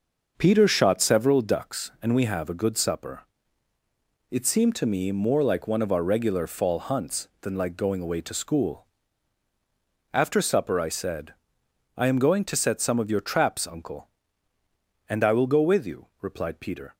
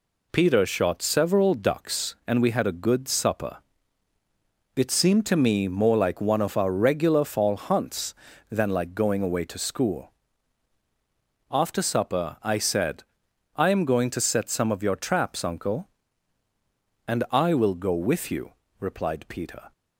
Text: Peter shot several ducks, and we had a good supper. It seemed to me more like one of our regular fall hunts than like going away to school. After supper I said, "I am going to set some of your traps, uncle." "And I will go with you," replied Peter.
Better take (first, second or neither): second